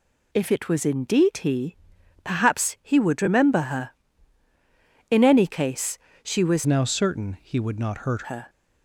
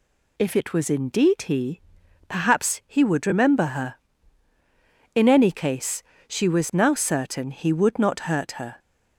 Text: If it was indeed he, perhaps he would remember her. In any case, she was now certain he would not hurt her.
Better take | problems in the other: second | changes voice from "now" to "hurt"; from 6.6 to 8.2 s; 1.6 s long

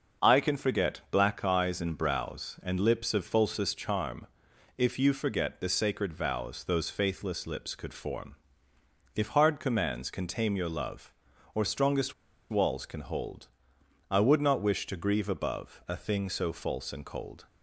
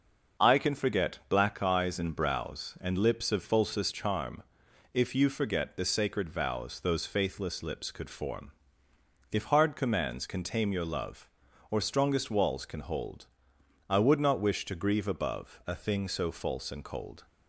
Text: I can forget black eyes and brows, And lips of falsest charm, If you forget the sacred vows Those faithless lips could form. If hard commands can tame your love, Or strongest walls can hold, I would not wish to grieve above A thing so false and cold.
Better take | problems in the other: second | starts louder than the rest; until 1.3 s; 6.5 dB; also in the second // pauses between "strongest" and "walls"; at 12.1 s; 0.38 s long

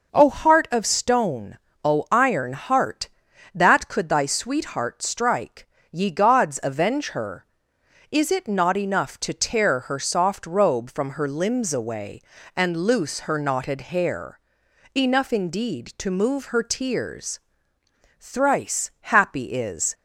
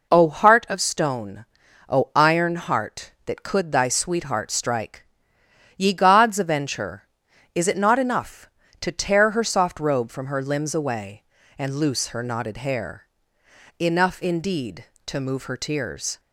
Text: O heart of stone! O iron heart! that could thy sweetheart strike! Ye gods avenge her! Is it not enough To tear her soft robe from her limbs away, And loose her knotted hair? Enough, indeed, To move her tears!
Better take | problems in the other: second | goes on to say "Thrice happy is"; strong; from 18.1 s on; 1.7 s long

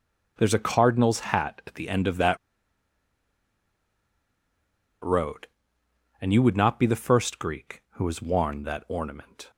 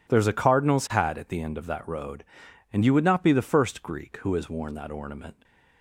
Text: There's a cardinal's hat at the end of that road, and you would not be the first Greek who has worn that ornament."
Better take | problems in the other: second | pauses between "that" and "road"; strong; at 2.3 s; 2.6 s long

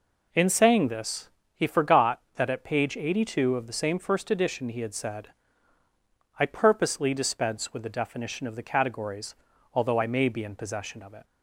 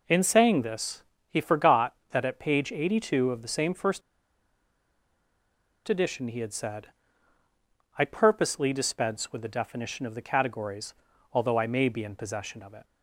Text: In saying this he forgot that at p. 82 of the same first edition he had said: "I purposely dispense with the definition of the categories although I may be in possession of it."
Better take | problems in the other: first | pauses between "this" and "he"; slight; at 1.0 s; 0.28 s long; slight in the first // pauses between "first" and "edition"; strong; at 4.0 s; 1.8 s long // pauses between "categories" and "although"; at 10.9 s; 0.40 s long; also in the first

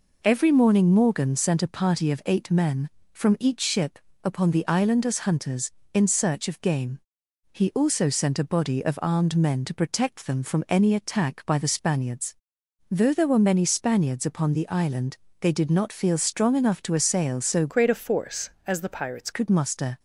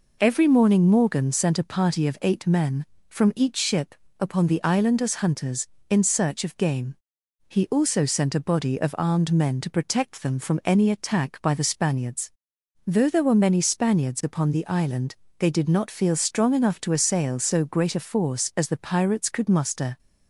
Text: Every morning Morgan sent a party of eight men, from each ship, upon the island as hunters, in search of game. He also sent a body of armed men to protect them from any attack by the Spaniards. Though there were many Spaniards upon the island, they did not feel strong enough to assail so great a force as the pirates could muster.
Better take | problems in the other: second | changes voice from "great" to "pirates"; from 17.6 to 19.3 s; 1.7 s long

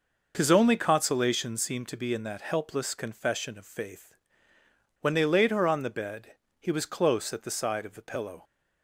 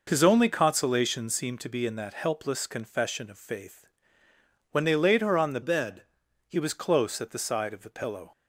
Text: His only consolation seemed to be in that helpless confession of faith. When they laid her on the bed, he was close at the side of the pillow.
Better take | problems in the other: first | changes voice from "bed" to "he"; from 5.6 to 6.5 s; 0.9 s long

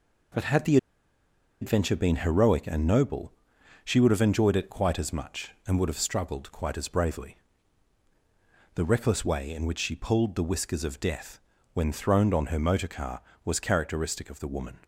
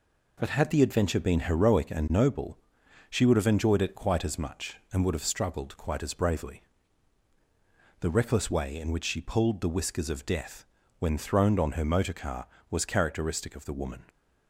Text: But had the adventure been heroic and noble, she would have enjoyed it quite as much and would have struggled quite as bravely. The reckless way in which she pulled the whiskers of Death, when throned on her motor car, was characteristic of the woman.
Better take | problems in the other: second | pauses between "the" and "adventure"; noticeable; at 0.7 s; 0.84 s long

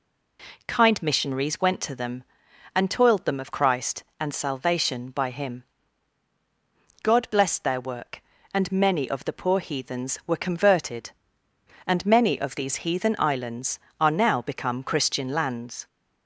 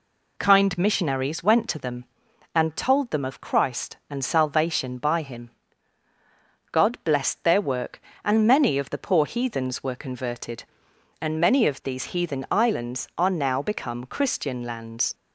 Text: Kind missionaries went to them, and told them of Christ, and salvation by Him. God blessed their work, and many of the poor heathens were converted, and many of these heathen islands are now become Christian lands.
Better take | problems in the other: second | says "toiled" for "told"; at 2.9 s

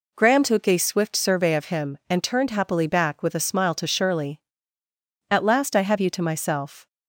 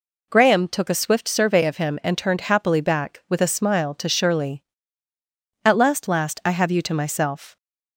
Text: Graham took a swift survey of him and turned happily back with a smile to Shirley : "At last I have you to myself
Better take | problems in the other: first | says "last" twice; at 6.0 s

